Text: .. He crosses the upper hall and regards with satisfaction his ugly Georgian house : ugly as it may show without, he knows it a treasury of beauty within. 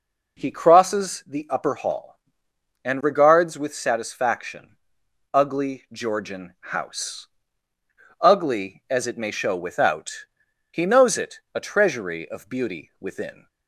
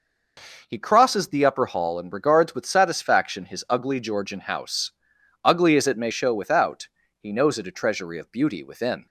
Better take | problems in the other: second | skips "his"; at 5.0 s

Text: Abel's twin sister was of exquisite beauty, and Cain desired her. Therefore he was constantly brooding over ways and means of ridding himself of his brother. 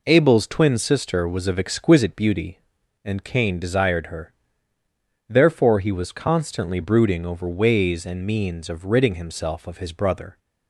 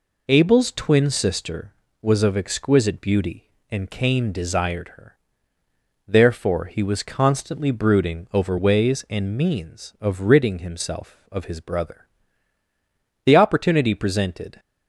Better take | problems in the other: first | goes on to say "The opportunity presented"; from 13.2 s on; 1.3 s long

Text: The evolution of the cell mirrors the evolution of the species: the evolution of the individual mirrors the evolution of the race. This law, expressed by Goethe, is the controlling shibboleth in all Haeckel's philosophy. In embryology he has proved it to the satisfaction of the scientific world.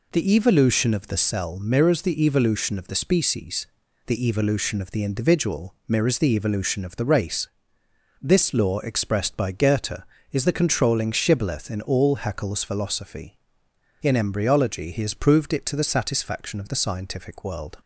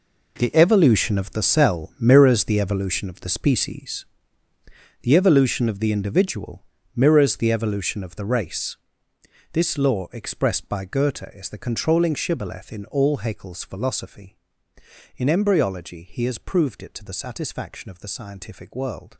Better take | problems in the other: first | gets quieter; strong; throughout; 13 dB // pauses between "individual" and "mirrors"; slight; at 6.6 s; 0.32 s long

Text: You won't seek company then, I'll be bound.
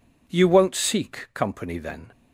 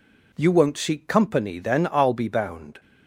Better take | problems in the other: second | stops before "I'll be bound"; at 2.1 s

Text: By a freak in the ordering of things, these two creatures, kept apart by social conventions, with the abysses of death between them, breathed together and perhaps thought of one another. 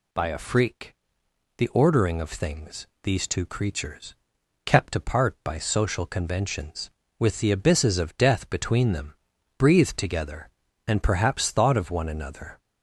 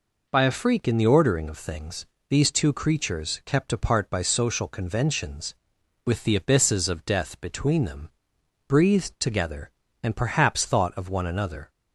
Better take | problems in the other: second | skips "in"; at 1.2 s

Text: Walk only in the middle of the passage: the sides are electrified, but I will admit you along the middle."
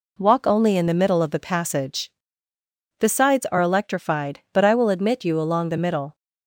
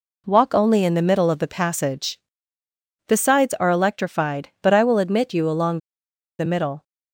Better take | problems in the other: first | pauses between "along" and "the"; noticeable; at 5.7 s; 0.59 s long

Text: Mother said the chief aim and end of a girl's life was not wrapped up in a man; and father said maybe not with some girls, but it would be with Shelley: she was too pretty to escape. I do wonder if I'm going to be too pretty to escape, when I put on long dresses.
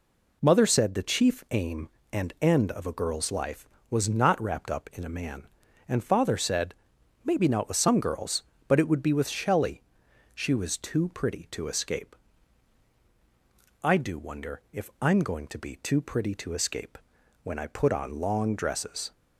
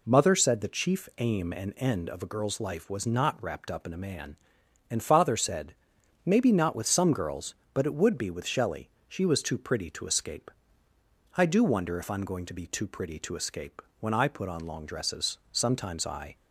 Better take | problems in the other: first | pauses between "said" and "maybe"; noticeable; at 5.7 s; 0.52 s long; noticeable in the first // goes on to say "Sometimes I"; noticeable; from 15.5 s on; 0.84 s long

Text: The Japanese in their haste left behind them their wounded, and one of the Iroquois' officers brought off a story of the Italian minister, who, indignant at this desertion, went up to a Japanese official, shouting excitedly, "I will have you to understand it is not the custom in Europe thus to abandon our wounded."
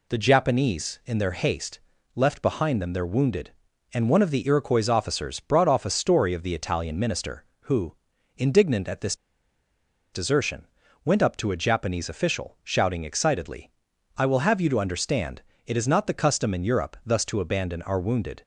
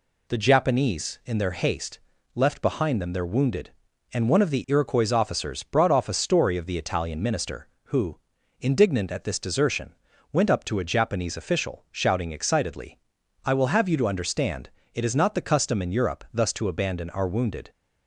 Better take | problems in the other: second | pauses between "haste" and "left"; slight; at 1.7 s; 0.36 s long; slight in the second // pauses between "this" and "desertion"; noticeable; at 9.1 s; 0.95 s long // pauses between "understand" and "it"; slight; at 15.4 s; 0.26 s long; slight in the second

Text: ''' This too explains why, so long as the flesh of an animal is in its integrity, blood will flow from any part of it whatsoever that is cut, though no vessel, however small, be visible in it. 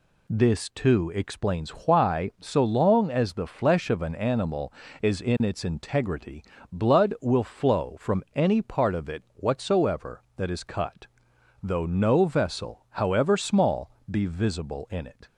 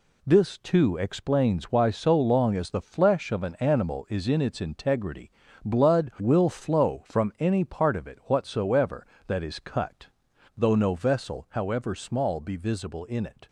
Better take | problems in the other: neither | none

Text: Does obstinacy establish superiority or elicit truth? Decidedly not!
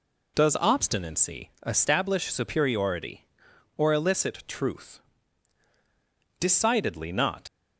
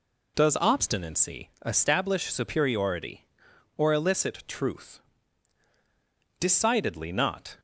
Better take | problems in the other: second | pauses between "obstinacy" and "establish"; slight; at 1.5 s; 0.16 s long; slight in the second // leaves "not" unfinished; at 7.4 s; 120 ms

